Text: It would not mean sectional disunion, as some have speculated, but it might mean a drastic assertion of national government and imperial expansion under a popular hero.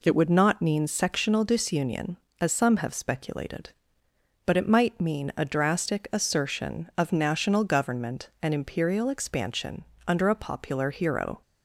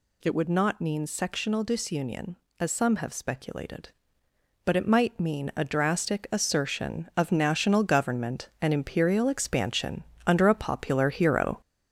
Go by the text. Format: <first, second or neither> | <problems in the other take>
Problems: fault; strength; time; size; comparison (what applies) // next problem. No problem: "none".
first | gets louder; noticeable; throughout; 4.5 dB // pauses between "expansion" and "under"; slight; at 10.0 s; 0.24 s long; slight in the first